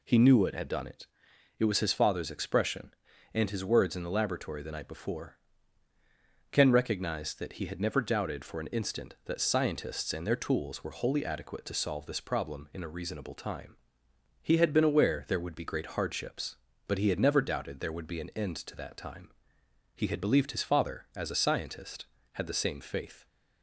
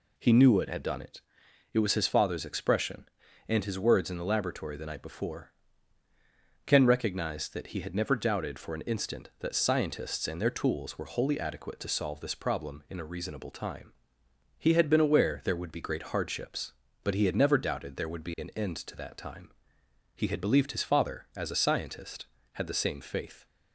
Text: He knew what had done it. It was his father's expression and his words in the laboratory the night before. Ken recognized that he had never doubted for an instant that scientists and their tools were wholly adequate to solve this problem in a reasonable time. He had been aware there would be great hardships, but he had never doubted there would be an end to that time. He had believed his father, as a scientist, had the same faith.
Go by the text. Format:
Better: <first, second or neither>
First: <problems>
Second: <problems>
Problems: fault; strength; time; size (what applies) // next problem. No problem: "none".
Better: neither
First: none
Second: none